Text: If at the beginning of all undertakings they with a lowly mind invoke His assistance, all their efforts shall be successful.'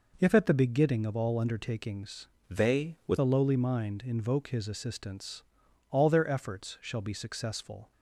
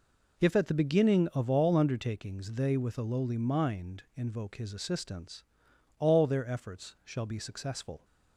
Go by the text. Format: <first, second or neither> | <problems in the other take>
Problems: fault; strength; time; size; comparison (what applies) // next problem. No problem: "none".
second | changes voice from "they" to "with"; from 2.4 to 3.1 s; 0.7 s long